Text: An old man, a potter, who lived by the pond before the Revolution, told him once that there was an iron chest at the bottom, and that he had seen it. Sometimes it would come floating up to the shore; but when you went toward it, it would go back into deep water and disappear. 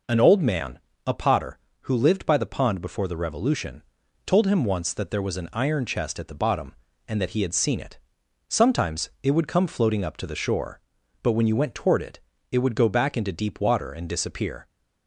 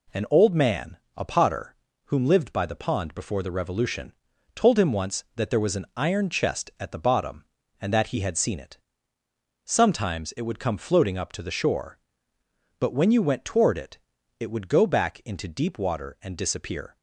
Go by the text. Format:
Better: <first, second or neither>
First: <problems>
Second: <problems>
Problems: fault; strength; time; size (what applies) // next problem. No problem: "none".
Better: first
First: none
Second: says "whom" for "who"; at 2.0 s